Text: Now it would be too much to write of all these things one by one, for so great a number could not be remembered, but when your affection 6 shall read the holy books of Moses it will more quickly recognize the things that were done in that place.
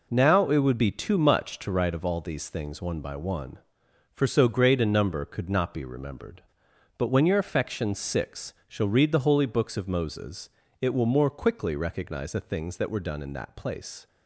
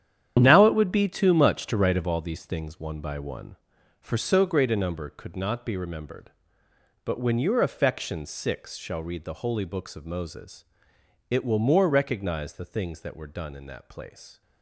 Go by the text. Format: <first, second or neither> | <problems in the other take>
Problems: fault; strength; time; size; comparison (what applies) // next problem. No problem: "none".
first | starts louder than the rest; strong; until 1.4 s; 9.5 dB // pauses between "Moses" and "it"; noticeable; at 10.6 s; 0.64 s long; slight in the first // skips "quickly"; at 11.9 s